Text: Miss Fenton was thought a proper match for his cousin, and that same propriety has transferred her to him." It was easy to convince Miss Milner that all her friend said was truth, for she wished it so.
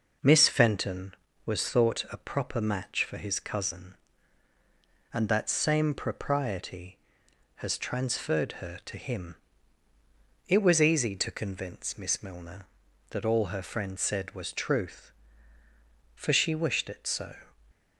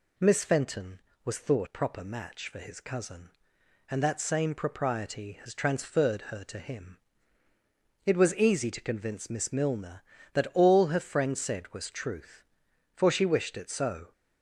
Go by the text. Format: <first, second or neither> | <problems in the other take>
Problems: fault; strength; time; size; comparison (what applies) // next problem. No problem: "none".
first | skips "a"; at 1.6 s